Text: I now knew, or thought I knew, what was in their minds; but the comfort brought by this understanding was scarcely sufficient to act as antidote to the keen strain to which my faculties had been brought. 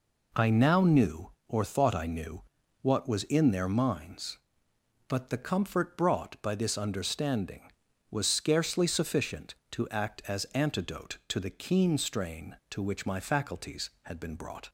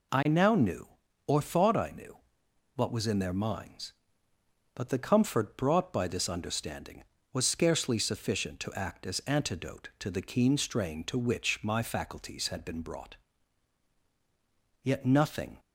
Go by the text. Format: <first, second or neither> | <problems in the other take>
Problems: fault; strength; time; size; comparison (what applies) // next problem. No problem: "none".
first | goes on to say "Yet nothing"; noticeable; from 14.8 s on; 0.76 s long